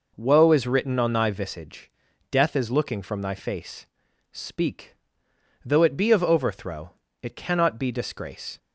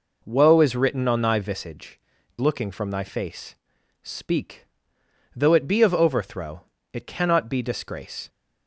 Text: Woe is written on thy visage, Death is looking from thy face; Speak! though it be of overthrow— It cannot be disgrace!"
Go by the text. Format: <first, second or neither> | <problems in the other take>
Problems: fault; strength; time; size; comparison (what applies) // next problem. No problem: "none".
first | skips "Death is"; at 2.1 s